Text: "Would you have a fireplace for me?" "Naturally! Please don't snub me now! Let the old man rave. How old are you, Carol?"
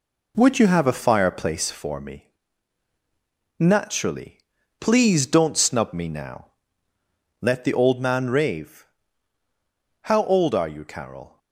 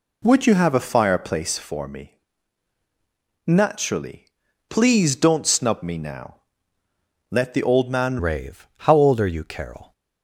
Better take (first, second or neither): first